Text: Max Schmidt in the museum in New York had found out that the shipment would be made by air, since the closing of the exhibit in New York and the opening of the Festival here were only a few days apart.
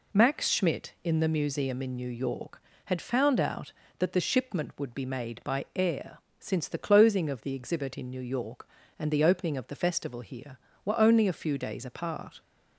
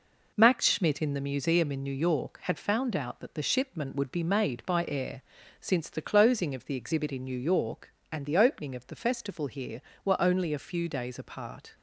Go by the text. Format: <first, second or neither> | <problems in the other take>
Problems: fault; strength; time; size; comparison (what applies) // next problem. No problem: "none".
neither | none